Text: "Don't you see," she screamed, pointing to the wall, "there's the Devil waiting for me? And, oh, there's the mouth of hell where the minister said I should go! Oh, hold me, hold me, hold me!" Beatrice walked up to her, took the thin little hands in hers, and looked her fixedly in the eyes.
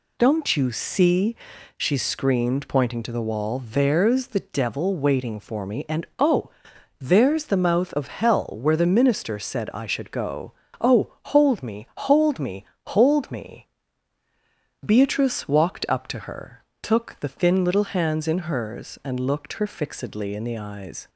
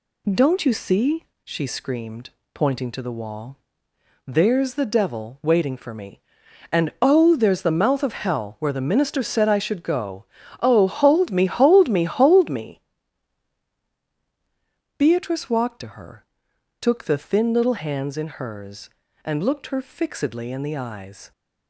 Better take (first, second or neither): first